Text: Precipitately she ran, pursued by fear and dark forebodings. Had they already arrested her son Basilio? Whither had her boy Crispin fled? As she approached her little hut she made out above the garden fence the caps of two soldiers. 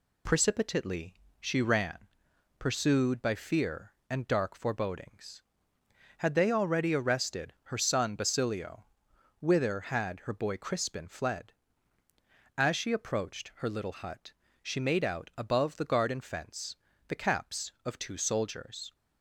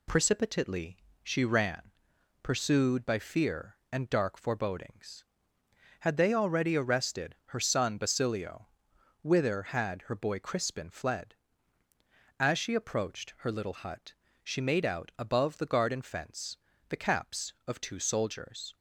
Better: neither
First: pauses between "Precipitately" and "she"; slight; at 1.1 s; 0.26 s long // pauses between "hut" and "she"; slight; at 14.3 s; 0.32 s long // pauses between "fence" and "the"; slight; at 16.7 s; 0.32 s long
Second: pauses between "Precipitately" and "she"; slight; at 0.9 s; 0.26 s long // pauses between "hut" and "she"; slight; at 14.1 s; 0.32 s long // pauses between "fence" and "the"; slight; at 16.5 s; 0.32 s long

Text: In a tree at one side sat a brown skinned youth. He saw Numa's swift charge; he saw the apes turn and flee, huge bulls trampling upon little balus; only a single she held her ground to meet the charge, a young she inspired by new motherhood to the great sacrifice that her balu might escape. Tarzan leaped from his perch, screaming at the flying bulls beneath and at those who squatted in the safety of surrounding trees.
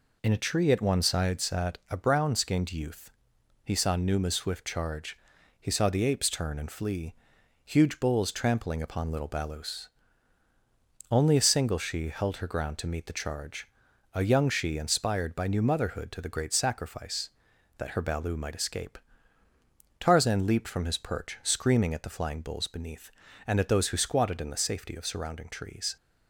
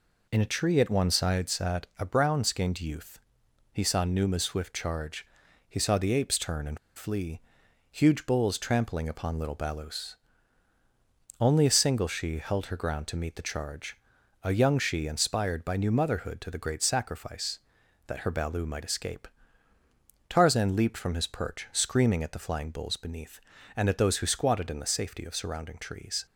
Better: first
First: none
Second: pauses between "and" and "flee"; slight; at 6.7 s; 0.18 s long

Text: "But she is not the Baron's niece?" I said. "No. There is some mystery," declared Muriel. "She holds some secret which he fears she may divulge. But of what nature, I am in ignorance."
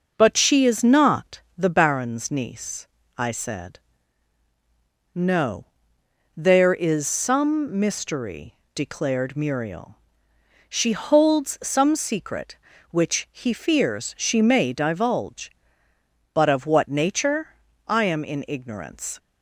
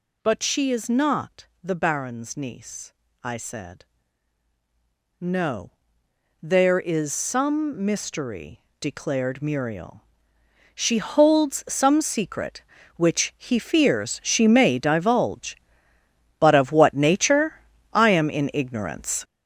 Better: first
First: pauses between "not" and "the"; slight; at 1.4 s; 0.16 s long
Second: gets louder; strong; throughout; 9 dB // pauses between "not" and "the"; slight; at 1.4 s; 0.16 s long

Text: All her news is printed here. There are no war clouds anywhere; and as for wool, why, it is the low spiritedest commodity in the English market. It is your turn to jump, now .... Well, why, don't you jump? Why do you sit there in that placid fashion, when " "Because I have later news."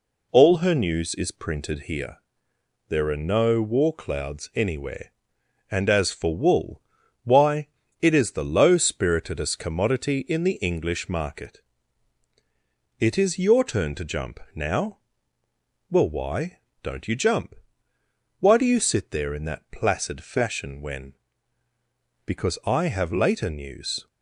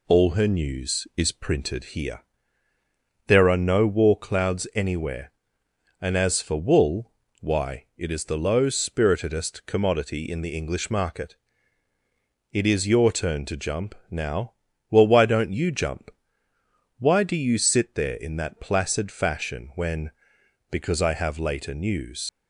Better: first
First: none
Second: leaves "news" unfinished; at 22.2 s; 135 ms

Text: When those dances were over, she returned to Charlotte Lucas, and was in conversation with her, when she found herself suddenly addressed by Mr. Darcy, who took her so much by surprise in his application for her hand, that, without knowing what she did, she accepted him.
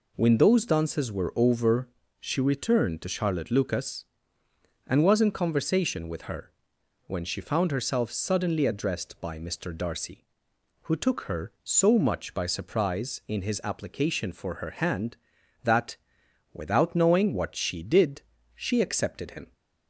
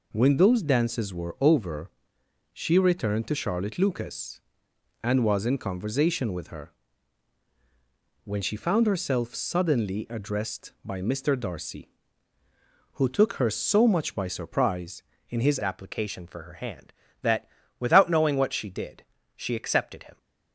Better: first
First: none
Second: changes voice at "application"; from 15.6 s on; 4.5 s long

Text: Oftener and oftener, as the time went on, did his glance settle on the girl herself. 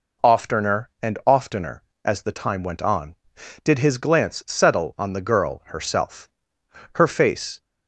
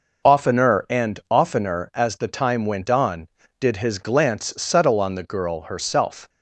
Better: second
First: goes on to say "Her face"; noticeable; from 6.9 s on; 0.64 s long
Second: none

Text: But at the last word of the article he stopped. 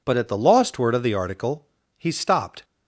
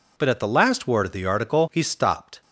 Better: second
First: says "lost" for "last"; at 0.3 s // pauses between "article" and "he"; slight; at 1.6 s; 0.30 s long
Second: none

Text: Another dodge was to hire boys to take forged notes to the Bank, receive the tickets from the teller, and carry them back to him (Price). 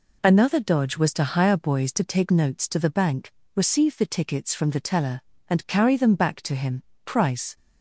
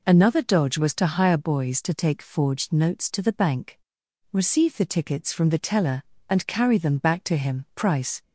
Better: second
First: skips "forged"; at 2.3 s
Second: none

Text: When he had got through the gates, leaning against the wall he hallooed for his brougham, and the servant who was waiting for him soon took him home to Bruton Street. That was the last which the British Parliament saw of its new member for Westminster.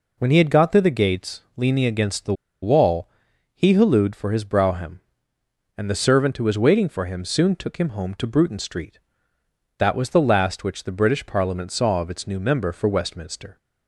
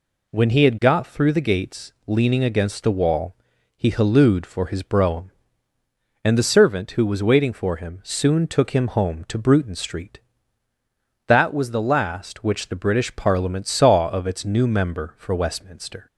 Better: second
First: pauses between "the" and "wall"; slight; at 2.3 s; 0.29 s long // pauses between "wall" and "he"; noticeable; at 3.0 s; 0.48 s long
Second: pauses between "wall" and "he"; at 3.3 s; 0.42 s long

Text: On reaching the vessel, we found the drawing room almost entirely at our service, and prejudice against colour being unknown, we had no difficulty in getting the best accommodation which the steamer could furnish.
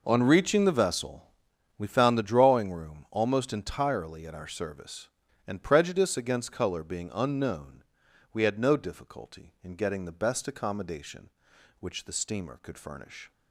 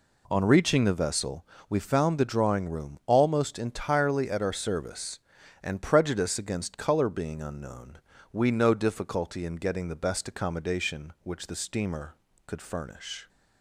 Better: first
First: none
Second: skips "had"; at 8.5 s

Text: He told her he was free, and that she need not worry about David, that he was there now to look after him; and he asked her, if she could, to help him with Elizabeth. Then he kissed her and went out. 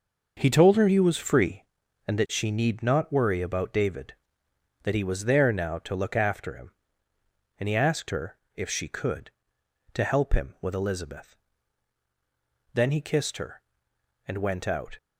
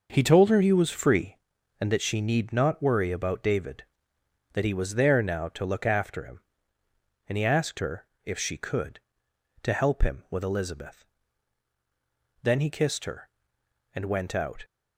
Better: neither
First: none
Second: none

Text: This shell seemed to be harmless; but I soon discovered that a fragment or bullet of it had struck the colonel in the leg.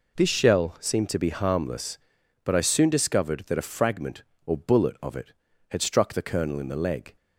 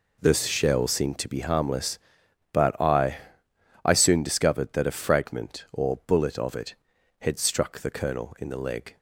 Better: first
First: none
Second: says "I" twice; at 3.8 s

